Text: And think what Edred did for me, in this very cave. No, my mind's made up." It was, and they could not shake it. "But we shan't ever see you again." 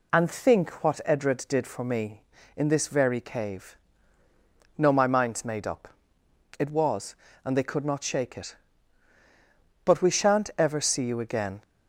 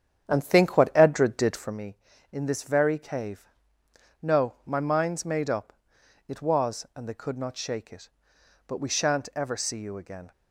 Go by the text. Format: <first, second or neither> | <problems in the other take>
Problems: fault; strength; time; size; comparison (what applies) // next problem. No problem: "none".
first | starts louder than the rest; strong; until 1.8 s; 9 dB